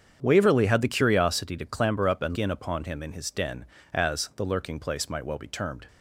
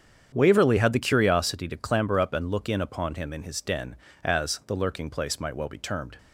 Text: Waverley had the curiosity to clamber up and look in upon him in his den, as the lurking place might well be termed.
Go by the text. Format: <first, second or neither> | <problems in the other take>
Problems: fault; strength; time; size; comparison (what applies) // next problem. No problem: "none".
second | starts louder than the rest; strong; until 1.2 s; 8 dB; strong in the second // skips "look"; at 2.3 s